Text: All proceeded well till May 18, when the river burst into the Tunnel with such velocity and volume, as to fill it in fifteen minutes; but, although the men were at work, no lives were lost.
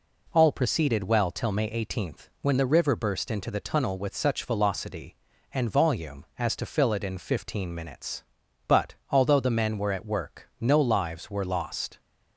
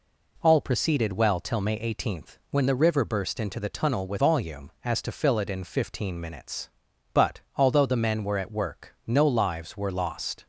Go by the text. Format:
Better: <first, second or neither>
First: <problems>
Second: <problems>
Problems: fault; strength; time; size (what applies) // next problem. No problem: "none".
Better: first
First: none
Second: skips "such velocity and"; at 4.1 s